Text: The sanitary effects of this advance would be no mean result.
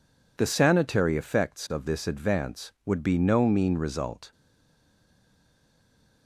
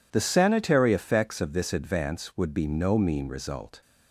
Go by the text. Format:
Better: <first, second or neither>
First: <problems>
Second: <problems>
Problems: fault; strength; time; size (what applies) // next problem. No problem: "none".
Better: second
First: stays silent after the last word; noticeable; from 4.3 s on; 1.9 s long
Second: none